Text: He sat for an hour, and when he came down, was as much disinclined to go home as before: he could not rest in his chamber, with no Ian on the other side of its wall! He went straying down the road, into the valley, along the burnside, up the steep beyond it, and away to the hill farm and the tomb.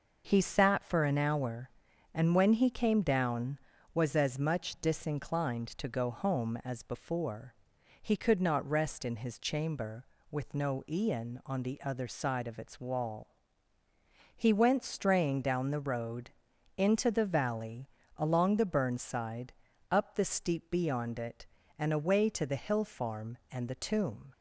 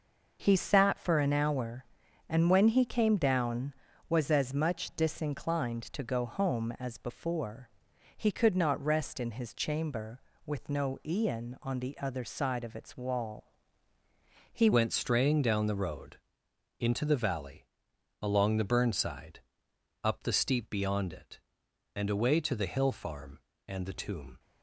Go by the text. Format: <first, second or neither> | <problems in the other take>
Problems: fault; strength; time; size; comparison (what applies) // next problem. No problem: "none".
first | changes voice at "went"; from 14.7 s on; 9.6 s long